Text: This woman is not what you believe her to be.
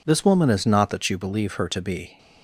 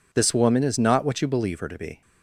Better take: second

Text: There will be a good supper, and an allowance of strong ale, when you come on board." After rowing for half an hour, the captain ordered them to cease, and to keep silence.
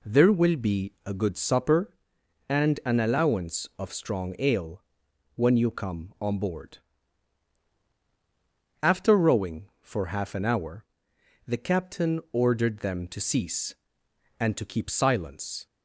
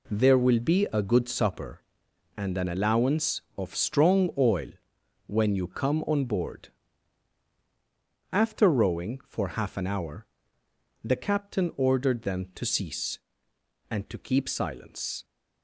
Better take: first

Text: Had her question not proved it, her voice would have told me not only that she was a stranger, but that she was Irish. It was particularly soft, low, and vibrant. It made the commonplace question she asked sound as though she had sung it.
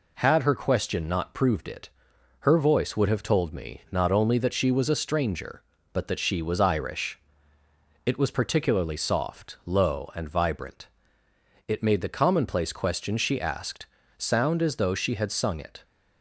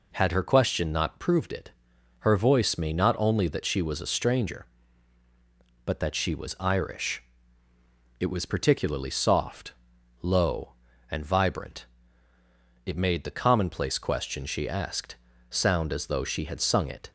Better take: first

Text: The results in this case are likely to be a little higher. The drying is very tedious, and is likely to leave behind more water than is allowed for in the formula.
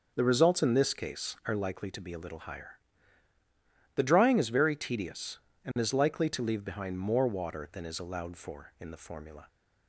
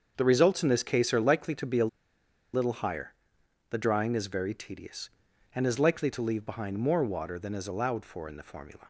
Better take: first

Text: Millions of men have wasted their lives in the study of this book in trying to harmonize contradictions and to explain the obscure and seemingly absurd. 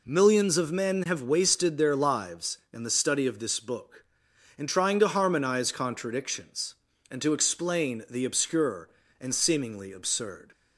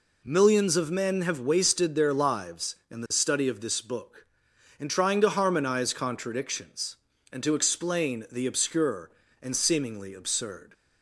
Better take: neither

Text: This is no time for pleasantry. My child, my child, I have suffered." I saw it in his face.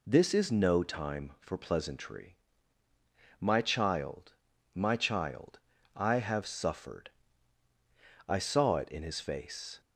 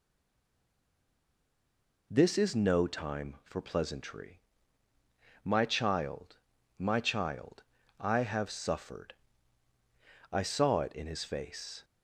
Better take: first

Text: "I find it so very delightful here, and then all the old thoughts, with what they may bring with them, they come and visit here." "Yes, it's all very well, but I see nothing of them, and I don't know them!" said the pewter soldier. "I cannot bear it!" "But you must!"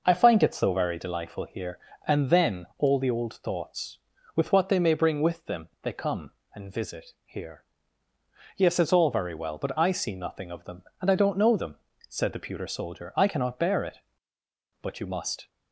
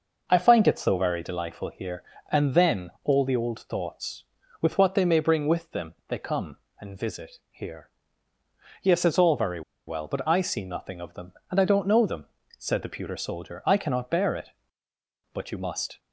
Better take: first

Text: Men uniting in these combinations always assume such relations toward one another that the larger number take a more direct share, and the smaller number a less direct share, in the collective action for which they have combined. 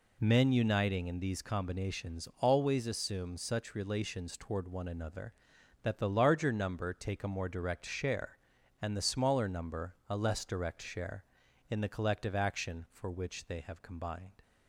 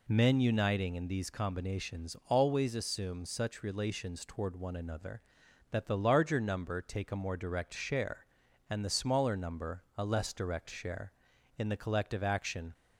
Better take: first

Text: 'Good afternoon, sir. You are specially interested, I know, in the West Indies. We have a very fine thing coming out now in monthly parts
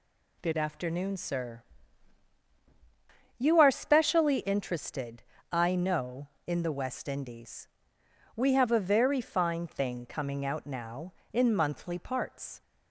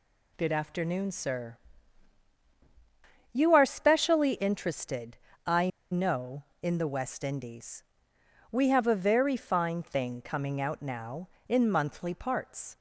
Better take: first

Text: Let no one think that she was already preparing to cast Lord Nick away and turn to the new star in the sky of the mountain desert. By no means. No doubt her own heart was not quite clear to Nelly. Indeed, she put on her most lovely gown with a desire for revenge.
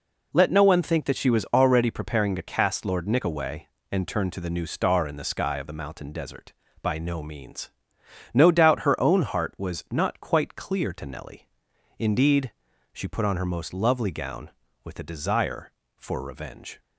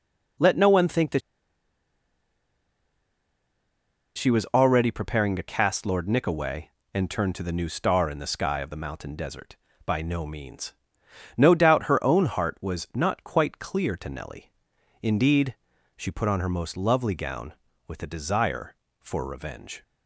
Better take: first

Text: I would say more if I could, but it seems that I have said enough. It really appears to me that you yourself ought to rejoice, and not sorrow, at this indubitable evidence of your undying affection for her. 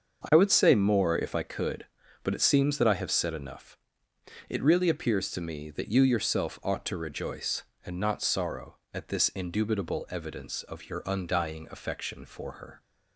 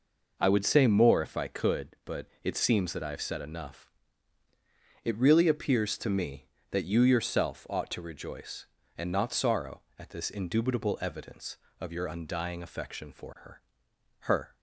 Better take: first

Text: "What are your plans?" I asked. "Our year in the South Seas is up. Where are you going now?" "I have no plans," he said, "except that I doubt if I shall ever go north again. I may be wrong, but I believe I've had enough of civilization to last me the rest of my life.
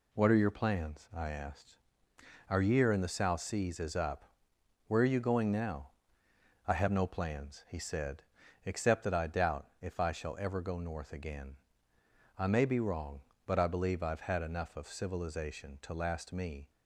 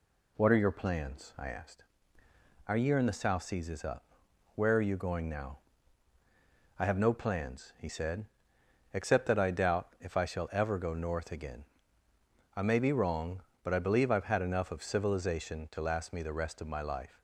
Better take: second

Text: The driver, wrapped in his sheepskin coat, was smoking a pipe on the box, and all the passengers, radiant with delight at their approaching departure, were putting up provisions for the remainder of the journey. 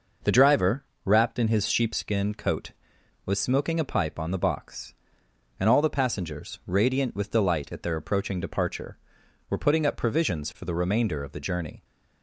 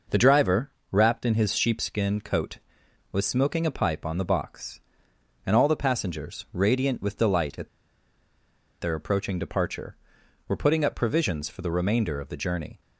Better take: first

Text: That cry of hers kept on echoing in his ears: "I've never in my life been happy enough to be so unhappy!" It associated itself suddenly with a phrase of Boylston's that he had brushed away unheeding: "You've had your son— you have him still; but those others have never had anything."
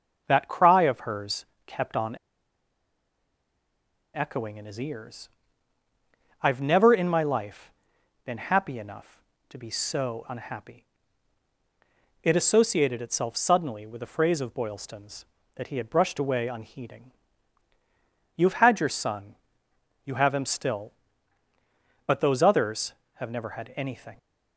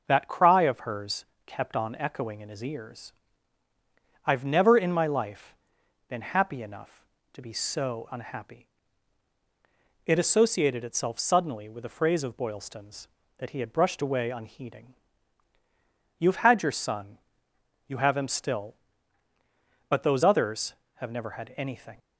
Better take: second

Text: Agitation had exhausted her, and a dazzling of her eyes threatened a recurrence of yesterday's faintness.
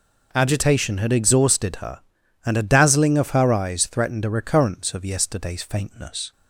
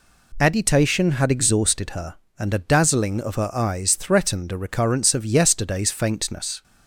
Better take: neither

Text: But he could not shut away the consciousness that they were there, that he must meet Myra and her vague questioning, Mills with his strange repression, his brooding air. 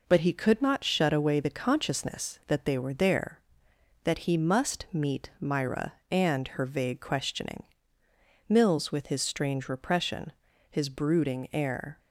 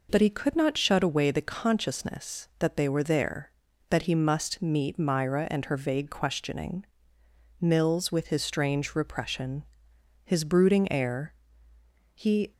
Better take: first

